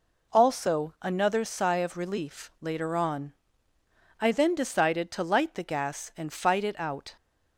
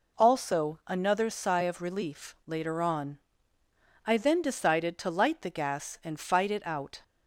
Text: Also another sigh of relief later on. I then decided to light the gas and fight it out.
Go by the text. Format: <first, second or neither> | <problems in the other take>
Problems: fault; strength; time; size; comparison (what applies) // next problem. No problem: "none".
neither | none